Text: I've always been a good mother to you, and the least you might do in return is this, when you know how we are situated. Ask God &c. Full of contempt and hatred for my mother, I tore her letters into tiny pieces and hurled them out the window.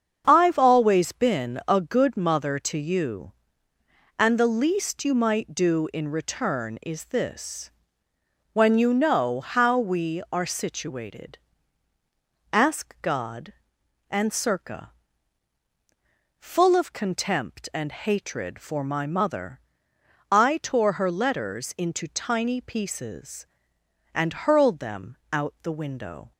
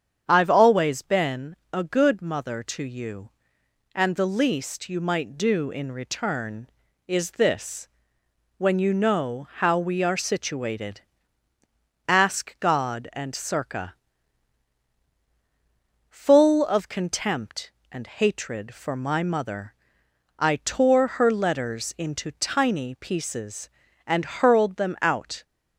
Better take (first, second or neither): first